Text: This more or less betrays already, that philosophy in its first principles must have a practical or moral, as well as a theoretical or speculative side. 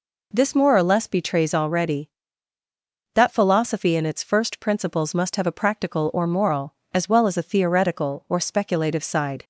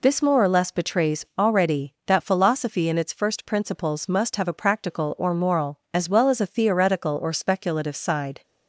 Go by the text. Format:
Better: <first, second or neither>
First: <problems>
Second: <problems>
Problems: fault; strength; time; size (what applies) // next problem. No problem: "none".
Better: neither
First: none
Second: none